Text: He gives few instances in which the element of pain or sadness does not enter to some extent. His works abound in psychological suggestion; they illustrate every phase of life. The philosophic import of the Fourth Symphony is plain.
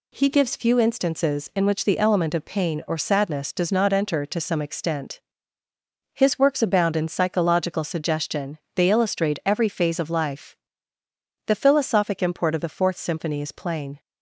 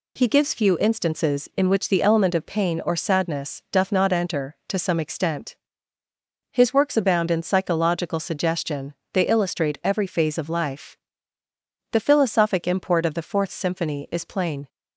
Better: first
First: none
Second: says "doth" for "does"; at 3.7 s

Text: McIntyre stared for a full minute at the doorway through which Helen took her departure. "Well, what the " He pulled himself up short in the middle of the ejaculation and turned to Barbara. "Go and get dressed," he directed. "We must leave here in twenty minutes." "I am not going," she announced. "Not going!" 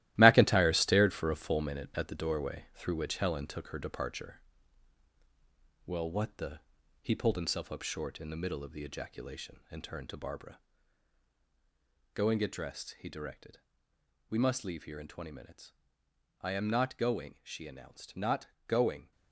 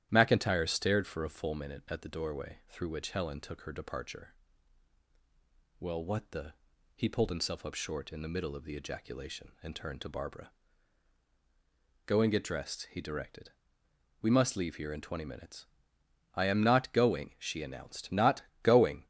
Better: second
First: gets quieter; strong; throughout; 8.5 dB // starts louder than the rest; strong; until 1.1 s; 15.5 dB // pauses between "Not" and "going"; slight; at 18.4 s; 0.20 s long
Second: starts louder than the rest; strong; until 1.1 s; 12 dB // pauses between "Not" and "going"; slight; at 18.4 s; 0.20 s long

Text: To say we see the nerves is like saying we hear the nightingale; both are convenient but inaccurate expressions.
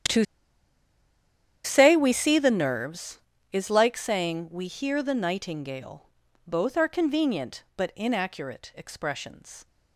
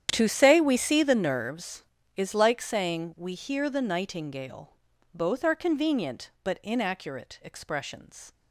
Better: second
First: starts louder than the rest; strong; until 2.5 s; 9.5 dB // pauses between "To" and "say"; strong; at 0.2 s; 1.4 s long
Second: starts louder than the rest; strong; until 1.1 s; 9.5 dB

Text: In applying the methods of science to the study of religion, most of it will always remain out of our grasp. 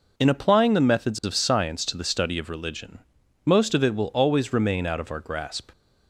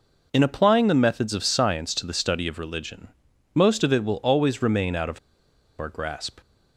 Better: first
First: none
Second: pauses between "of" and "our"; noticeable; at 5.1 s; 0.60 s long

